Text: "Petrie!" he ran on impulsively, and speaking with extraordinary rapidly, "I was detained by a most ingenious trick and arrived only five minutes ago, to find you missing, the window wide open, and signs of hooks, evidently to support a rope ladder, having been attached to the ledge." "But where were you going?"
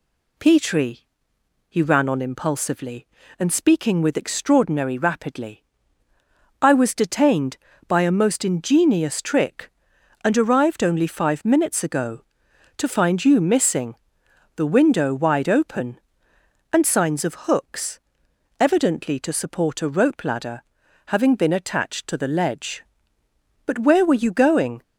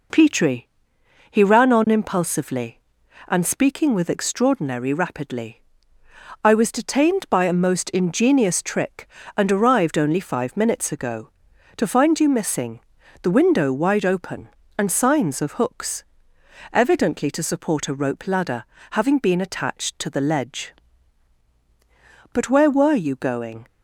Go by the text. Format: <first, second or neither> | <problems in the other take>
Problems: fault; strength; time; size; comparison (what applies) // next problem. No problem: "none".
neither | none